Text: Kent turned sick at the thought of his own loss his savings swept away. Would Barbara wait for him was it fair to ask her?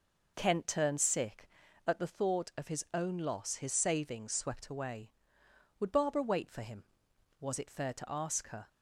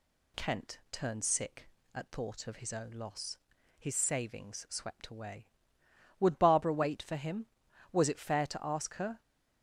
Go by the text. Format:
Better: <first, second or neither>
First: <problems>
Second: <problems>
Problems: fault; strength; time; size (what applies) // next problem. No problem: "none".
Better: first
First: none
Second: skips "the"; at 2.1 s // pauses between "loss" and "his"; at 3.3 s; 0.42 s long